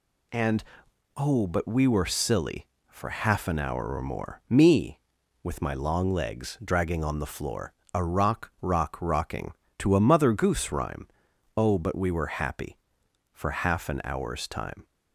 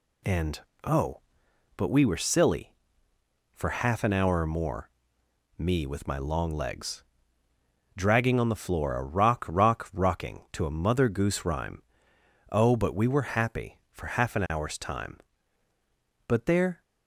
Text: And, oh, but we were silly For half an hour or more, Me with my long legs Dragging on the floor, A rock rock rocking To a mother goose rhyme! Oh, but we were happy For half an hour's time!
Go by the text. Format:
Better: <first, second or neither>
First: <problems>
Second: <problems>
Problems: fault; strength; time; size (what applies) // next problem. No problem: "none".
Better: first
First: none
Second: pauses between "legs" and "Dragging"; noticeable; at 7.0 s; 0.92 s long // goes on to say "But there"; from 16.2 s on; 0.54 s long